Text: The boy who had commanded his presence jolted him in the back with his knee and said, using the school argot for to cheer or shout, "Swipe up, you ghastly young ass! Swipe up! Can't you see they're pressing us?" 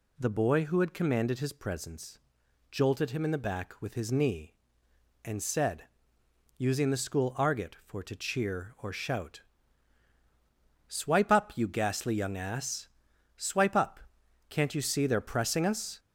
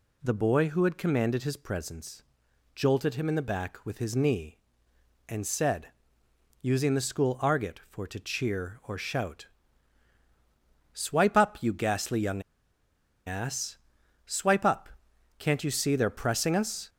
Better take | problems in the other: first | pauses between "presence" and "jolted"; noticeable; at 2.2 s; 0.54 s long; noticeable in the first // pauses between "young" and "ass"; noticeable; at 12.4 s; 0.84 s long

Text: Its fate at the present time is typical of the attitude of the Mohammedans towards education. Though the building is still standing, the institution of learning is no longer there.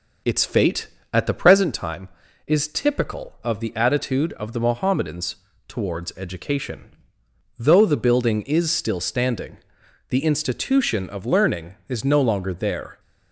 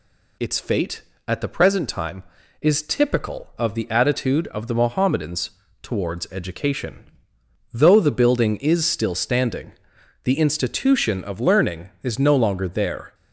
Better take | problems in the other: second | starts louder than the rest; noticeable; until 1.8 s; 5.5 dB // pauses between "Mohammedans" and "towards"; slight; at 5.3 s; 0.32 s long; slight in the second

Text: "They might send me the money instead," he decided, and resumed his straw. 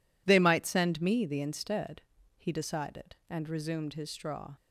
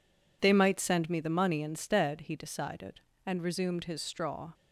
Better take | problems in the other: second | skips "money"; at 1.4 s

